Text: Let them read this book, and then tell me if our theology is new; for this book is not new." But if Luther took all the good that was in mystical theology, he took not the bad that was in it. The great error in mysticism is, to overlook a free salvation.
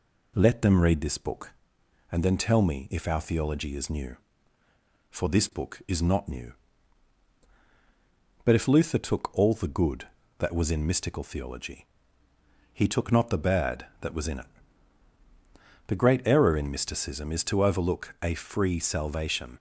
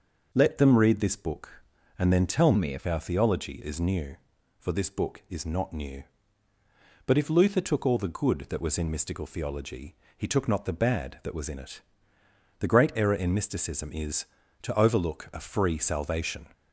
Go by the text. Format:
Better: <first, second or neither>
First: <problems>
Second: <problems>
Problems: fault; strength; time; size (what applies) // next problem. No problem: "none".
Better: first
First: none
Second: starts louder than the rest; noticeable; until 1.3 s; 6 dB // changes voice from "me" to "if"; from 2.5 to 2.8 s; 0.3 s long